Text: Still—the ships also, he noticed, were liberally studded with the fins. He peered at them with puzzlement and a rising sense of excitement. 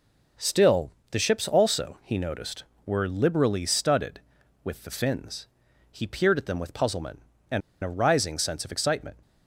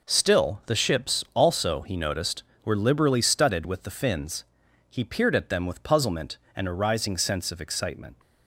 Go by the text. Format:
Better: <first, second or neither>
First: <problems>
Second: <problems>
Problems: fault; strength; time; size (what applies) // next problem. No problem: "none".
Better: second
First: pauses between "and" and "a"; slight; at 7.6 s; 0.23 s long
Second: none